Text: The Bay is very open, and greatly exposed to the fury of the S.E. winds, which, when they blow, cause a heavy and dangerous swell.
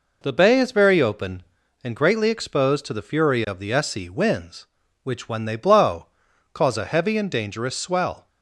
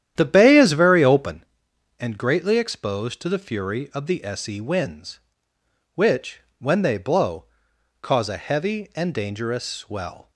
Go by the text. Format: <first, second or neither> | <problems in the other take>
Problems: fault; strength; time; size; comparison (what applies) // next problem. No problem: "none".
first | starts louder than the rest; strong; until 1.5 s; 10.5 dB